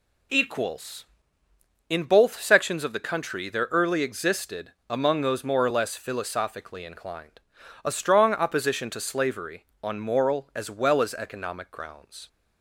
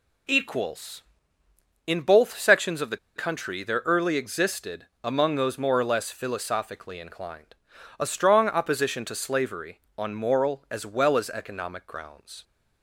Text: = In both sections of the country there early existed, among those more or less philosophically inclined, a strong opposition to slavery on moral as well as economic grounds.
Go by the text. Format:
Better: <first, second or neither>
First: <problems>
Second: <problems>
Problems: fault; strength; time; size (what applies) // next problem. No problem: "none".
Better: first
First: none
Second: pauses between "the" and "country"; slight; at 2.9 s; 0.19 s long